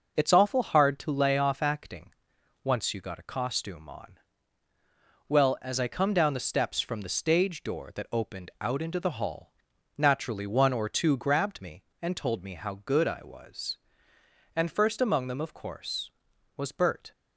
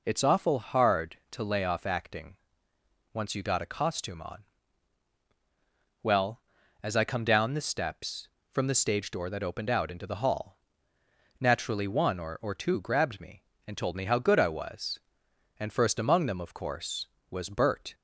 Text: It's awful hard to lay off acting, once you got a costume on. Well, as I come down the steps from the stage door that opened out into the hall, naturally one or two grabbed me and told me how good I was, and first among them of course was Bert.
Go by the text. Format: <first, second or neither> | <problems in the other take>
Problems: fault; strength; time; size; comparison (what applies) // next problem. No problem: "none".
first | says "or" twice; at 12.4 s